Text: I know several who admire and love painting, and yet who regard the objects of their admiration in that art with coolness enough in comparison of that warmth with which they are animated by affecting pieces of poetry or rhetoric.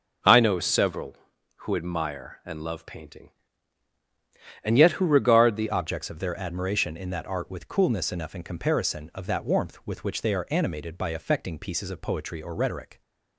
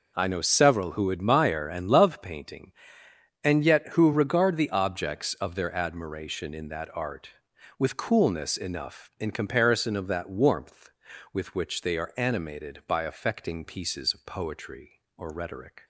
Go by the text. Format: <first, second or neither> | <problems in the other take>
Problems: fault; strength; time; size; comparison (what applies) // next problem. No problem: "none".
second | changes voice at "objects"; from 5.7 s on; 7.3 s long